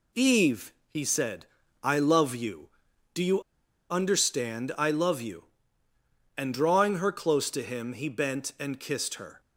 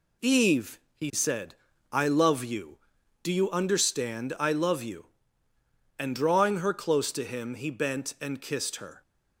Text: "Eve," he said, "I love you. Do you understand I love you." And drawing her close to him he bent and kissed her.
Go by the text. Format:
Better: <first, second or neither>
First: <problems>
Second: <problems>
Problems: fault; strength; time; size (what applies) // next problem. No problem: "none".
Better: second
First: pauses between "you" and "understand"; noticeable; at 3.4 s; 0.49 s long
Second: none